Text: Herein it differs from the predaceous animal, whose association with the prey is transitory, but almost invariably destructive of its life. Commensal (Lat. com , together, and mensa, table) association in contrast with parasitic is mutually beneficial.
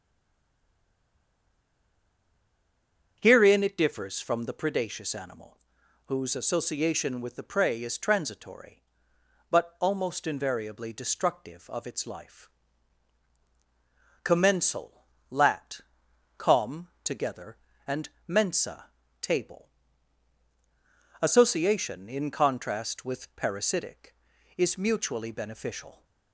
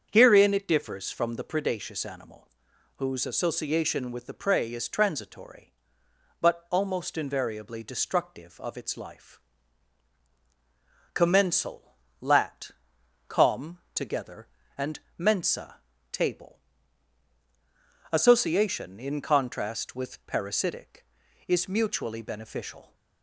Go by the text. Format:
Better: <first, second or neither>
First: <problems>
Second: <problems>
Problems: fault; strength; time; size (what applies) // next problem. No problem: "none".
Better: second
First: stays silent before the first word; strong; until 3.1 s; 3.1 s long // starts louder than the rest; strong; until 4.2 s; 7.5 dB // pauses between "and" and "mensa"; slight; at 18.0 s; 0.20 s long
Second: starts louder than the rest; strong; until 1.1 s; 7.5 dB // pauses between "and" and "mensa"; slight; at 14.9 s; 0.20 s long